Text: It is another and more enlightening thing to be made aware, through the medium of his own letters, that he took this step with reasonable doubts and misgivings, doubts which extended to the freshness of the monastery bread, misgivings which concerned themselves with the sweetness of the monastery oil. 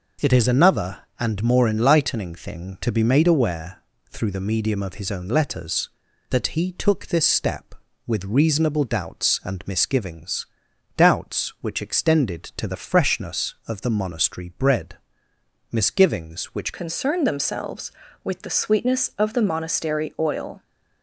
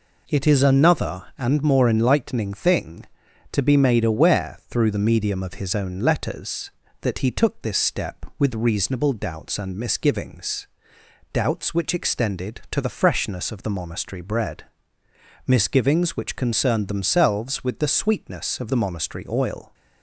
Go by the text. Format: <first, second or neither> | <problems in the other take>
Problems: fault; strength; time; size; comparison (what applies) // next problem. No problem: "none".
second | changes voice at "concerned"; from 16.7 s on; 3.9 s long